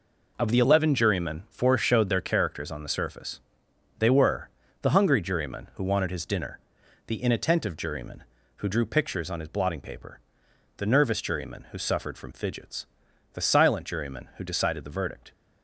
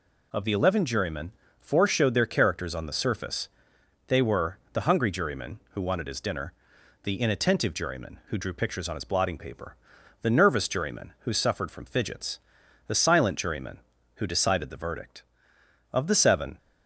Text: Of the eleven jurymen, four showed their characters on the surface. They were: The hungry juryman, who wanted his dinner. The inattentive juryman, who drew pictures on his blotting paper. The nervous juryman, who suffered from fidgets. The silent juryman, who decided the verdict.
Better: first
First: none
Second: goes on to say "Of the seven"; noticeable; from 15.9 s on; 0.64 s long

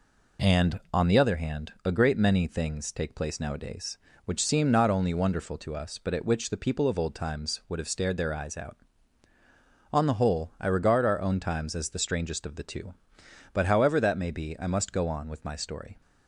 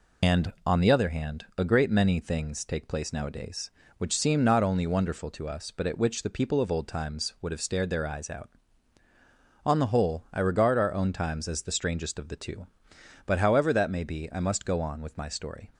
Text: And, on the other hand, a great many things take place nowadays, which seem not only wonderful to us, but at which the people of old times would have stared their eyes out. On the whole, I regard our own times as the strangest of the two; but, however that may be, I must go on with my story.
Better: first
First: none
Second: loses the start of "And"; at 0.2 s; 105 ms

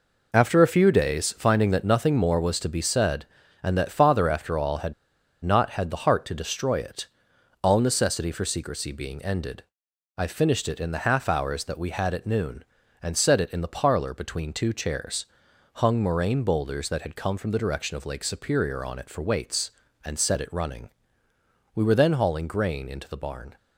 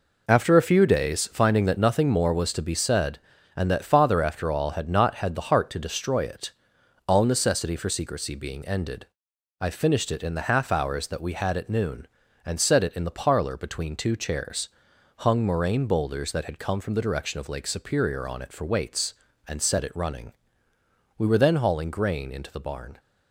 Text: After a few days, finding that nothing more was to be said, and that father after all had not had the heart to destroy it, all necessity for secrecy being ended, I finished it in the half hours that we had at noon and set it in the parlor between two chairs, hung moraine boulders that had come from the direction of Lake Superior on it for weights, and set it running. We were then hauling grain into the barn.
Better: second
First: pauses between "had" and "not"; noticeable; at 4.9 s; 0.50 s long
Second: none

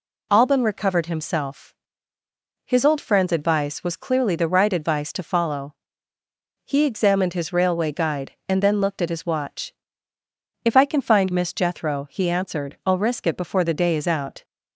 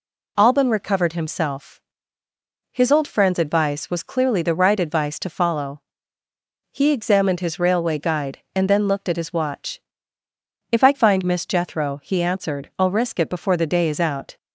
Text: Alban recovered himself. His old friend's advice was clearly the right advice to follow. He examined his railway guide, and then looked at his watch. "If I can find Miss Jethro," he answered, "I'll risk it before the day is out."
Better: first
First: none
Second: skips "can"; at 10.9 s

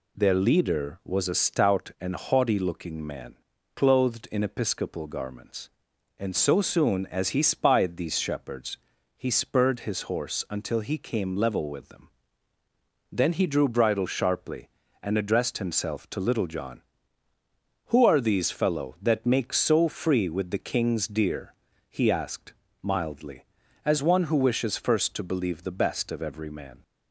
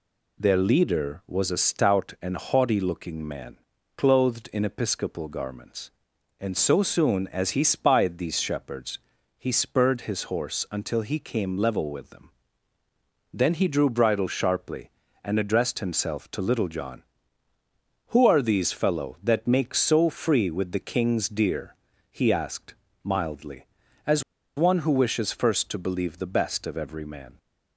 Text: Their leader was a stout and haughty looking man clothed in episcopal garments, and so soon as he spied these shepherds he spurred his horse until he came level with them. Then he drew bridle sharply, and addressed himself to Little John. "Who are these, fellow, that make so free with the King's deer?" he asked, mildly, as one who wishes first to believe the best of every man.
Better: first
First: pauses between "man" and "clothed"; at 3.3 s; 0.38 s long // pauses between "shepherds" and "he"; slight; at 8.7 s; 0.36 s long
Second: pauses between "man" and "clothed"; at 3.5 s; 0.38 s long // pauses between "shepherds" and "he"; slight; at 8.9 s; 0.36 s long // pauses between "as" and "one"; slight; at 24.2 s; 0.34 s long

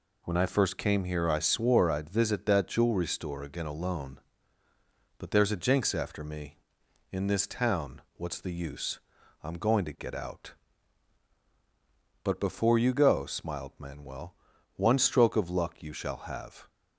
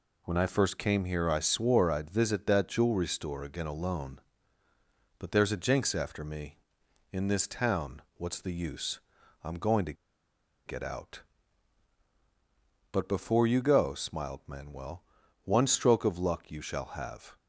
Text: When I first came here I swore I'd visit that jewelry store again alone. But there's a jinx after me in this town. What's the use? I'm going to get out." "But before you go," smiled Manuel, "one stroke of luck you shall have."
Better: first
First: none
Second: pauses between "to" and "get"; noticeable; at 9.9 s; 0.73 s long

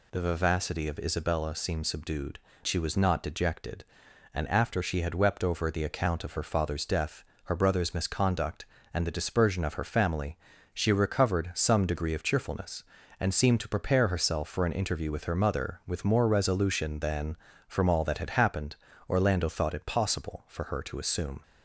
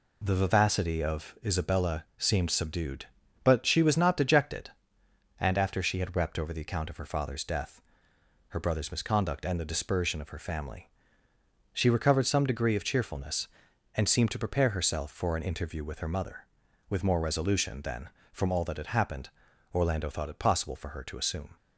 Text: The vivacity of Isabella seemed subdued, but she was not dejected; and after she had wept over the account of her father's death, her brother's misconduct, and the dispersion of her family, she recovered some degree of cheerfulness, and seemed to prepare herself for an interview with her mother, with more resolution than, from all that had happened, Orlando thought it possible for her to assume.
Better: second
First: skips "but"; at 2.5 s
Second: none

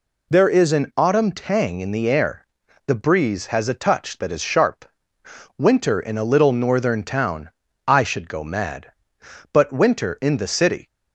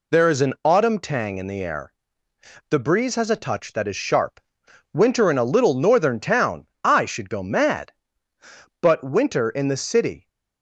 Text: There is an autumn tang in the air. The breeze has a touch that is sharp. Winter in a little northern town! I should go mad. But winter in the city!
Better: neither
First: none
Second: none

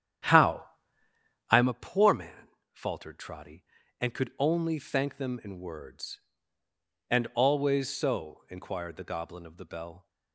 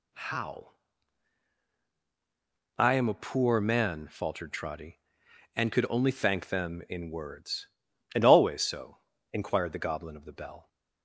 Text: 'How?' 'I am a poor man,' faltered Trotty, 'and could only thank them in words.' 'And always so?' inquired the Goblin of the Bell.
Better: second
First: starts louder than the rest; strong; until 1.7 s; 10 dB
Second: none

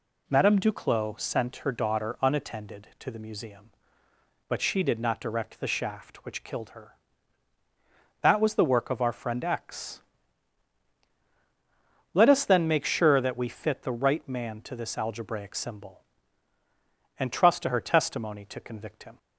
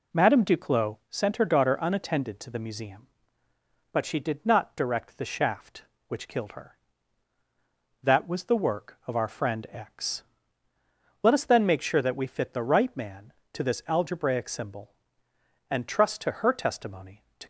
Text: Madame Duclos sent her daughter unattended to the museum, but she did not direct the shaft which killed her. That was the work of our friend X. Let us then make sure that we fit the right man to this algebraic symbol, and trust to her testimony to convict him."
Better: first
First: none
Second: stops before "convict him"; at 17.4 s

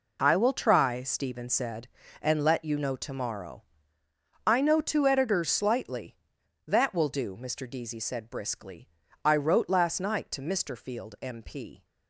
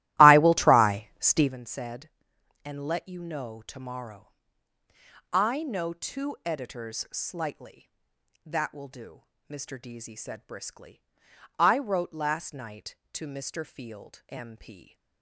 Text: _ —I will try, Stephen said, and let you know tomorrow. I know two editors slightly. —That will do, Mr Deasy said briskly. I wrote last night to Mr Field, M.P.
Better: first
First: none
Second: starts louder than the rest; strong; until 1.5 s; 16 dB

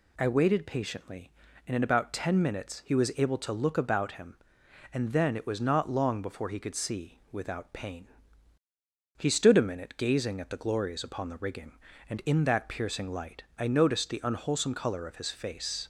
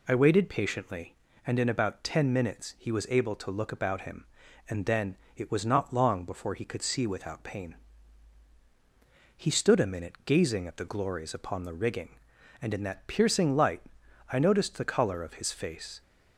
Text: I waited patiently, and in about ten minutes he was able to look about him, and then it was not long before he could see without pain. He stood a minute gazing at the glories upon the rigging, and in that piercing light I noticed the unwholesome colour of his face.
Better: first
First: pauses between "light" and "I"; slight; at 13.4 s; 0.16 s long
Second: pauses between "then" and "it"; slight; at 5.1 s; 0.20 s long // pauses between "light" and "I"; noticeable; at 13.8 s; 0.52 s long // skips "unwholesome"; at 14.8 s

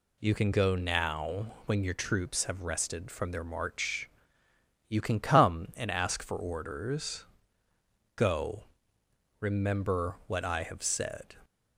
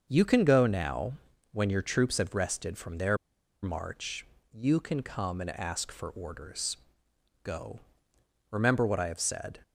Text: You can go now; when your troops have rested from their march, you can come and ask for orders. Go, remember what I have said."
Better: first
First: none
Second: starts louder than the rest; until 1.1 s; 6.5 dB // pauses between "their" and "march"; noticeable; at 3.1 s; 0.47 s long

